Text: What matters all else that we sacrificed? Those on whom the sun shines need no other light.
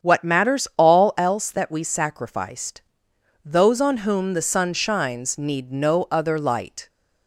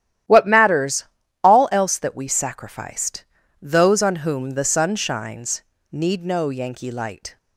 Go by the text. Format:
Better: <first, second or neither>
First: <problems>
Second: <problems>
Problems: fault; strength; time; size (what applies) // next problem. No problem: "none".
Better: first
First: starts louder than the rest; strong; until 1.1 s; 8 dB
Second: starts louder than the rest; strong; until 1.6 s; 12 dB // pauses between "matters" and "all"; slight; at 1.0 s; 0.36 s long // pauses between "shines" and "need"; slight; at 5.6 s; 0.28 s long // says "yankee" for "other"; at 6.4 s